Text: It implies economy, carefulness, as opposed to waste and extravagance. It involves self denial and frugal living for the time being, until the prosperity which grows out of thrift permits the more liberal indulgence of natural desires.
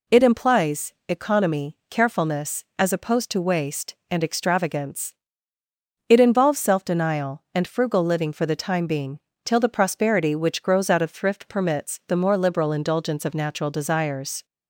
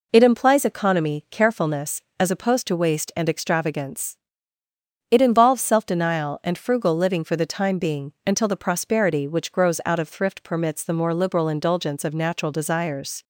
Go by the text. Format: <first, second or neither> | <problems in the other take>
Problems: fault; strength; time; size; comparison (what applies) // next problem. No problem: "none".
second | pauses between "implies" and "economy"; slight; at 0.9 s; 0.16 s long // says "till" for "until"; at 9.4 s